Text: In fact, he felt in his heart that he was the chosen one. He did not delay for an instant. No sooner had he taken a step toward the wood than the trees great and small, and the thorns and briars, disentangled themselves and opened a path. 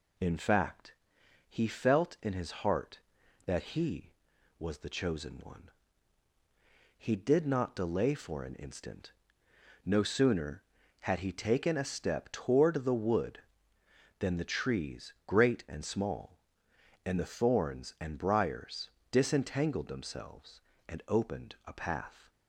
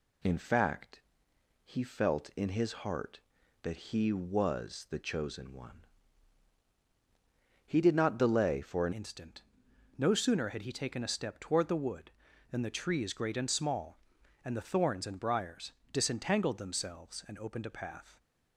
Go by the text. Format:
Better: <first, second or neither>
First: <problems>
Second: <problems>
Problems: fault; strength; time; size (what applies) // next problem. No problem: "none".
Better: first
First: none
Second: changes voice at "instant"; from 8.9 s on; 9.2 s long